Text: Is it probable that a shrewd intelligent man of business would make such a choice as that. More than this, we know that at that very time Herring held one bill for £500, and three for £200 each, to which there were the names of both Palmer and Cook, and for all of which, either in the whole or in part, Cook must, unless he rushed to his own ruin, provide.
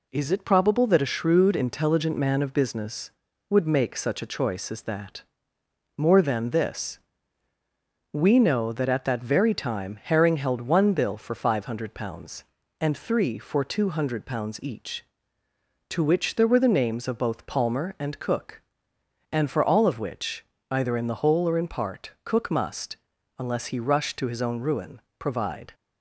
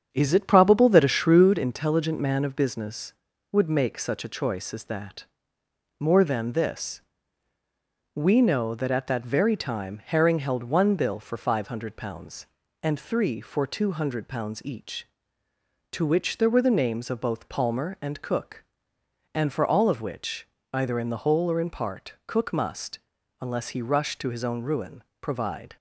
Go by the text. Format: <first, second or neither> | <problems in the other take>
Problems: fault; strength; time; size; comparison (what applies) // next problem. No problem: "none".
first | starts louder than the rest; strong; until 1.5 s; 8 dB